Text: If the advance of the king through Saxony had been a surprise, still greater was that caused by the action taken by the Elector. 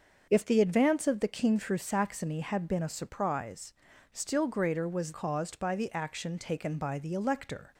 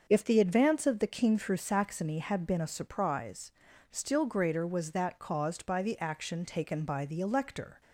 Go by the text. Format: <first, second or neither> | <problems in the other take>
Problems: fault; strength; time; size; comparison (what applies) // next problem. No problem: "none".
second | starts louder than the rest; until 1.3 s; 6.5 dB; also in the second // skips "that"; at 5.1 s